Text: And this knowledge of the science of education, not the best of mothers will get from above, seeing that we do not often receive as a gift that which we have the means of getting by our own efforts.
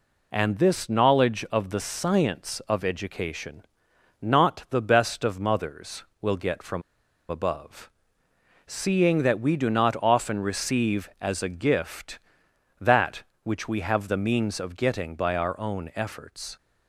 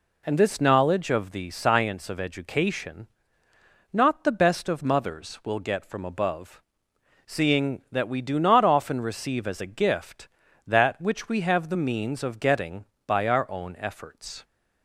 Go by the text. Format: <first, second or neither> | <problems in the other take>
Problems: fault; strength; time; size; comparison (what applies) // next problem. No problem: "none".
second | pauses between "from" and "above"; noticeable; at 6.8 s; 0.47 s long